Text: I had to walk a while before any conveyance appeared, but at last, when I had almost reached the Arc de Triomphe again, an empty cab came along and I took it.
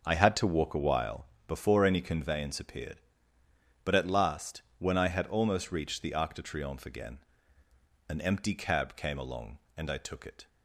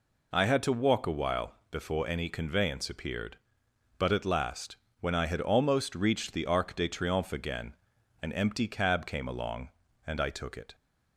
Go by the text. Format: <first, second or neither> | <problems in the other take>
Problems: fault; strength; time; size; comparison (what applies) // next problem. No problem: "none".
second | starts louder than the rest; noticeable; until 1.4 s; 6 dB // pauses between "while" and "before"; slight; at 1.2 s; 0.18 s long; slight in the second